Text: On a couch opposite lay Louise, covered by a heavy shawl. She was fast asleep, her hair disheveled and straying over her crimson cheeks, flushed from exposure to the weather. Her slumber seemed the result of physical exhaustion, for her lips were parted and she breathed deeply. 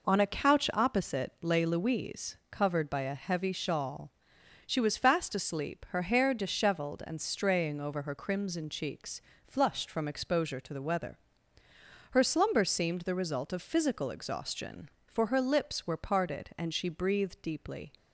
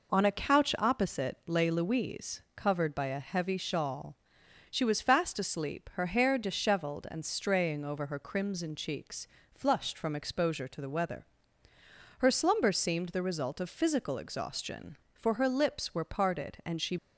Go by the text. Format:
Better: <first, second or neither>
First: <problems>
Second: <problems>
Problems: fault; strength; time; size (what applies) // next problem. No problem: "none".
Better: first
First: none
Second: stops before "breathed deeply"; at 16.9 s